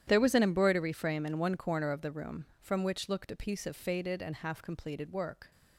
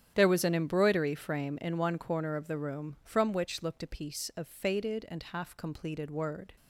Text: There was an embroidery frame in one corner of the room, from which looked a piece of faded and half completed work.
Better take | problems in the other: first | starts louder than the rest; strong; until 1.1 s; 10 dB; strong in the first // says "word" for "work"; at 6.1 s

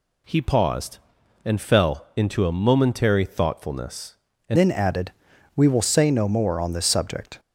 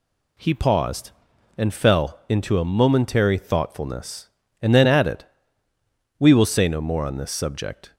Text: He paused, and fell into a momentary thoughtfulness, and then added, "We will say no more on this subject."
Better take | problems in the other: second | changes voice at "then"; from 4.5 s on; 2.8 s long

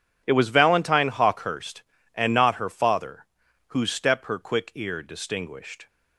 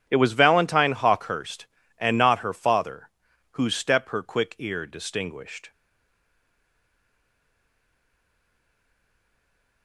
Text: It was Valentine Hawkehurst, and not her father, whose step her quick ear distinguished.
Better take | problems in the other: first | stays silent after the last word; strong; from 5.7 s on; 4.1 s long

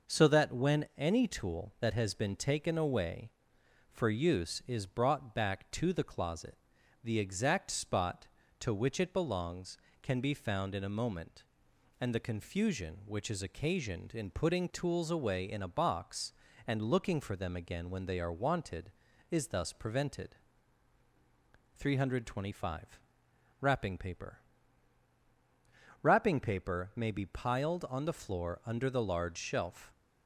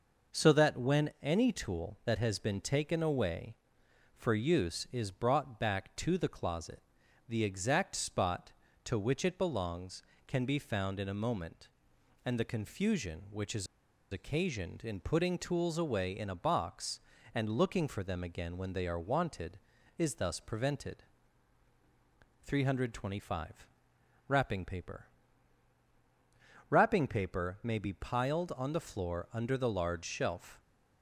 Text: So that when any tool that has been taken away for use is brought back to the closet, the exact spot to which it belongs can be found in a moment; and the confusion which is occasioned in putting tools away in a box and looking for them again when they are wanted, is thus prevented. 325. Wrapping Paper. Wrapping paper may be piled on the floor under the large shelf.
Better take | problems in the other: first | pauses between "is" and "occasioned"; at 13.6 s; 0.45 s long

